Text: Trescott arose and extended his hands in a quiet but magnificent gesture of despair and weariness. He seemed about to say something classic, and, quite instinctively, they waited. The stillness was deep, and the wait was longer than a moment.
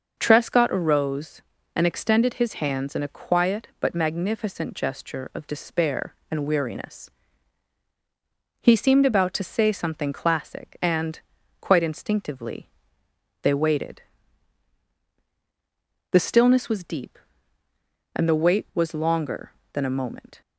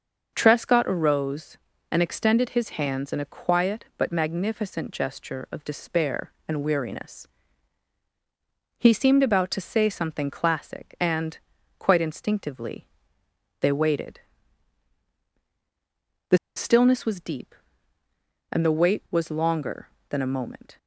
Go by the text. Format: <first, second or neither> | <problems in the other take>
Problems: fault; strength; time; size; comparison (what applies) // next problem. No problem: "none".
first | pauses between "The" and "stillness"; slight; at 16.3 s; 0.19 s long